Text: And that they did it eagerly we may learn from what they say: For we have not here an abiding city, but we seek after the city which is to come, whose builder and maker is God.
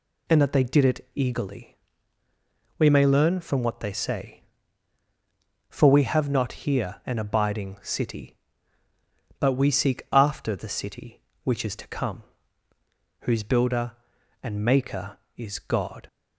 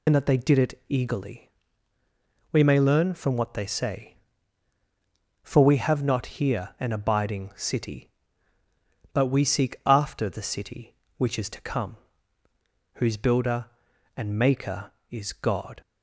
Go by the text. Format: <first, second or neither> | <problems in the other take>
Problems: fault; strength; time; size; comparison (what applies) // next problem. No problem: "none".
first | loses the start of "And"; at 0.0 s; 40 ms // pauses between "eagerly" and "we"; at 1.5 s; 1.0 s long; also in the first